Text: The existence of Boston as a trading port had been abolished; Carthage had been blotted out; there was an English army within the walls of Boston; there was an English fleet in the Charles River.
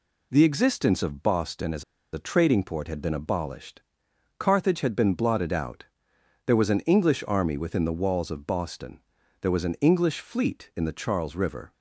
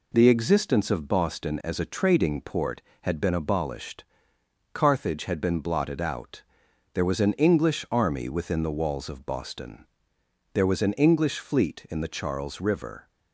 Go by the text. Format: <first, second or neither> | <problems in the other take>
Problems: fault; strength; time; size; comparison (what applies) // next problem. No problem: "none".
second | pauses between "as" and "a"; slight; at 1.8 s; 0.29 s long